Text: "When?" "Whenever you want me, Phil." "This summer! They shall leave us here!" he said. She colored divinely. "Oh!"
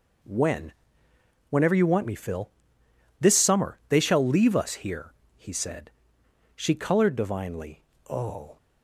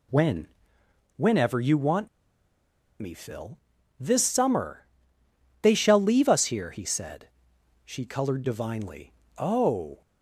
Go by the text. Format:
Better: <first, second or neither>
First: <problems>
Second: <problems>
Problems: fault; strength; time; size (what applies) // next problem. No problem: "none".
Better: first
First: none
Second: pauses between "want" and "me"; noticeable; at 2.0 s; 0.92 s long